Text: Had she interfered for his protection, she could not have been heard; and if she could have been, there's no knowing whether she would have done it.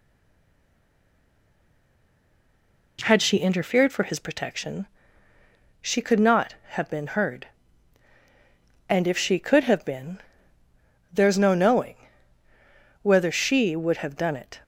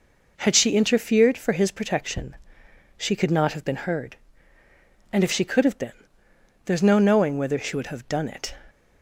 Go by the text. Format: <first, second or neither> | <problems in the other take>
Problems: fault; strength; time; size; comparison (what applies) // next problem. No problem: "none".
second | stays silent before the first word; strong; until 2.9 s; 2.9 s long // pauses between "knowing" and "whether"; at 11.9 s; 1.0 s long